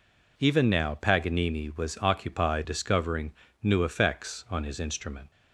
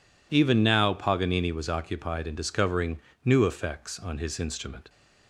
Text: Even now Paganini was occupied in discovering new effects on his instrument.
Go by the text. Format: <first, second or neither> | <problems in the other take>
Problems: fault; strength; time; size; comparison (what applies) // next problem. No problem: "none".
second | skips "in"; at 2.6 s // pauses between "discovering" and "new"; slight; at 3.3 s; 0.32 s long; slight in the second